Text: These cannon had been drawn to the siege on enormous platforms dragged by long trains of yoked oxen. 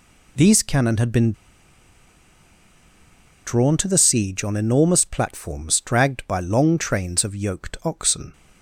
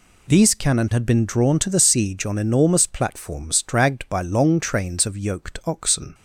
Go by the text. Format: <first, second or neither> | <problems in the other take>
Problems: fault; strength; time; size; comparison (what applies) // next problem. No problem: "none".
second | pauses between "been" and "drawn"; strong; at 1.3 s; 2.1 s long